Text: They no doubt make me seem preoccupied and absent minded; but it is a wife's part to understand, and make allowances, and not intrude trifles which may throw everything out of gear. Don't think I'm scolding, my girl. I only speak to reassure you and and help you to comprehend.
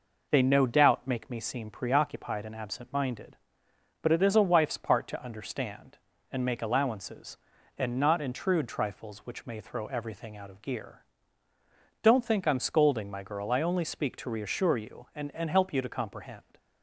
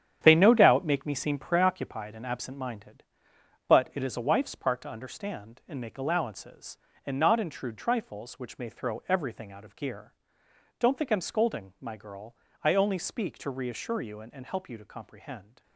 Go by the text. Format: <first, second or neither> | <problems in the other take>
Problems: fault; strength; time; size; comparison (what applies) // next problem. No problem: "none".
first | gets quieter; strong; throughout; 9 dB